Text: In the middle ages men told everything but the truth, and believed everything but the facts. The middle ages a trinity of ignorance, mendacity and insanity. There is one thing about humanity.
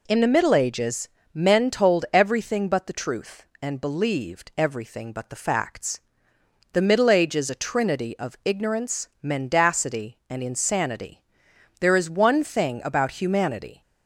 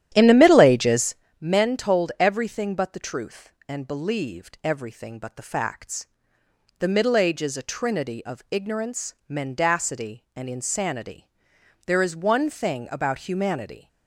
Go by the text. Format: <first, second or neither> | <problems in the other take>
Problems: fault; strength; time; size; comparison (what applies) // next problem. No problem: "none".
first | starts louder than the rest; strong; until 1.3 s; 11.5 dB // pauses between "ages" and "men"; slight; at 1.1 s; 0.26 s long; slight in the first